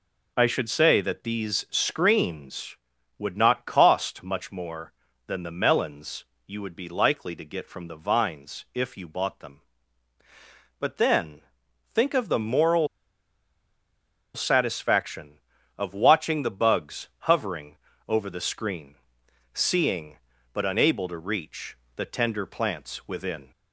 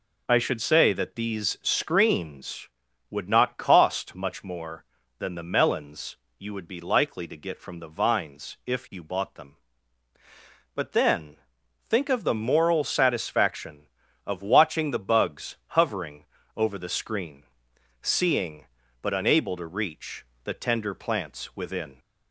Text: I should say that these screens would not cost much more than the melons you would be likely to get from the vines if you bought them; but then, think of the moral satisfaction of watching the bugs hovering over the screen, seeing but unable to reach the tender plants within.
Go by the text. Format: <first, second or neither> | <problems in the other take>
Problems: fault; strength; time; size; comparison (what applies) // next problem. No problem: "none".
second | pauses between "melons" and "you"; slight; at 6.2 s; 0.22 s long; slight in the second // pauses between "moral" and "satisfaction"; strong; at 12.8 s; 1.4 s long // pauses between "hovering" and "over"; slight; at 17.7 s; 0.32 s long; slight in the second // pauses between "reach" and "the"; slight; at 21.7 s; 0.18 s long; slight in the second